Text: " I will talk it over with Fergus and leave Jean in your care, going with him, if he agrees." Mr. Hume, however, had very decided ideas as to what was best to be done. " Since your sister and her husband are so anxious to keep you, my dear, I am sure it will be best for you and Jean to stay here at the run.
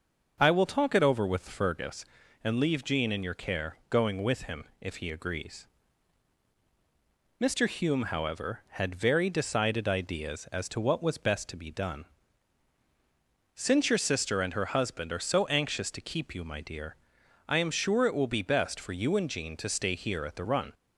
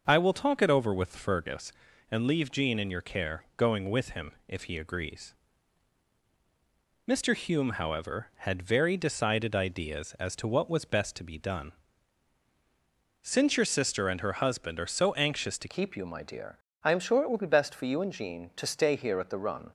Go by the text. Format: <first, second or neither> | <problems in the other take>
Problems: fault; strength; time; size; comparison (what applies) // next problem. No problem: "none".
first | starts louder than the rest; until 1.0 s; 6.5 dB; also in the first // changes voice at "keep"; from 15.6 s on; 4.1 s long